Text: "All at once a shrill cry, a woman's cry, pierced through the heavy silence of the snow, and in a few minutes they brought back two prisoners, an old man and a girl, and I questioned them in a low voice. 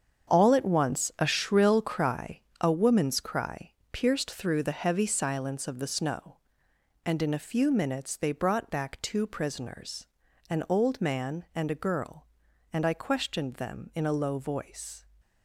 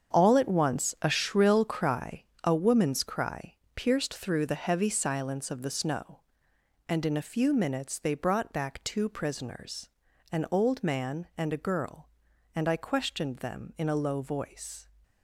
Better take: neither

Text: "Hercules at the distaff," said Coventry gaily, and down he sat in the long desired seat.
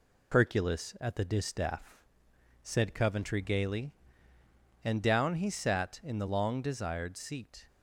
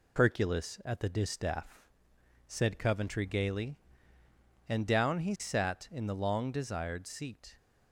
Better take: neither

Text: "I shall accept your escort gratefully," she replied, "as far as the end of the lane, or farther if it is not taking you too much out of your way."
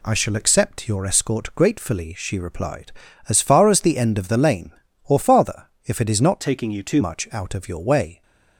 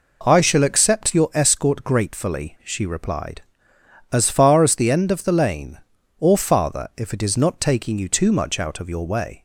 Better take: second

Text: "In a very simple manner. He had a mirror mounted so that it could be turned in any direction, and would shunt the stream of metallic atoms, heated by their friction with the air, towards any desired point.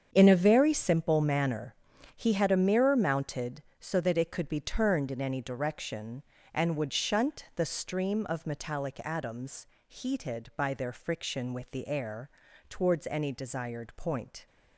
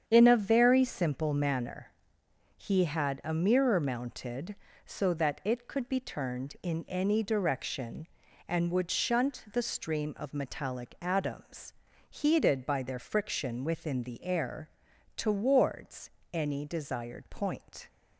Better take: first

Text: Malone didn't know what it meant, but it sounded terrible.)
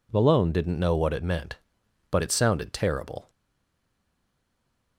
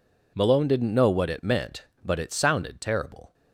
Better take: second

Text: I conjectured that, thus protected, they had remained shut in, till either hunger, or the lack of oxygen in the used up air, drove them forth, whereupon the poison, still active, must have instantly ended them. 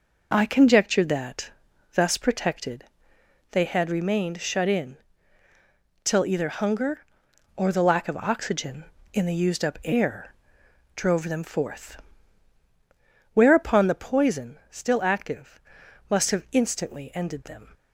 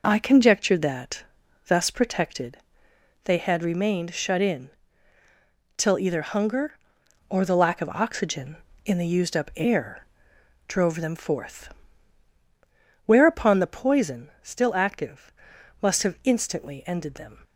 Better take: neither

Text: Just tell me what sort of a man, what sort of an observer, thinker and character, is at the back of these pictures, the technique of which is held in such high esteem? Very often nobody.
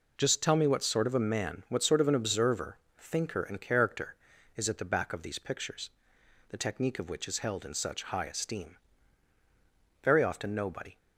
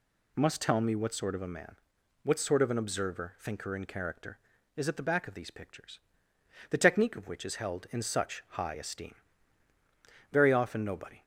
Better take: first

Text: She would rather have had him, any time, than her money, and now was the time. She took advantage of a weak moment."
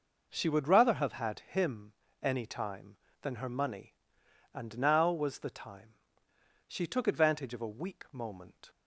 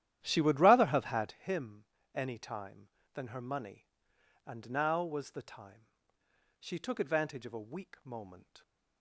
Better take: first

